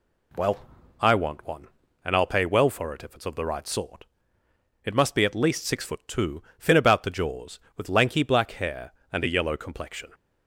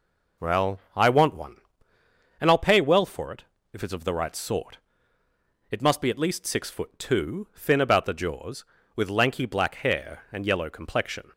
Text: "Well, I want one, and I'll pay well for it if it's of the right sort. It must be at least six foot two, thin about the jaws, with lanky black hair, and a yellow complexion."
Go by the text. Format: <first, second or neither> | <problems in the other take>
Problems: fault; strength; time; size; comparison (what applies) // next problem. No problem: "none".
first | pauses between "it" and "if"; slight; at 3.4 s; 0.28 s long // skips "a"; at 10.4 s